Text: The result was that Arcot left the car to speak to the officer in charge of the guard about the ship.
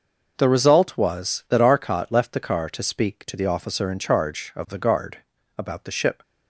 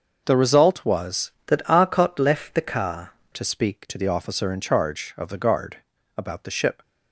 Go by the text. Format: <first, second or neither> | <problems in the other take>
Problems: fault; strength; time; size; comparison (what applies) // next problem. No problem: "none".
first | starts louder than the rest; until 1.2 s; 6 dB // changes voice from "that" to "car"; from 1.4 to 3.1 s; 1.7 s long // pauses between "guard" and "about"; at 5.7 s; 0.40 s long; also in the first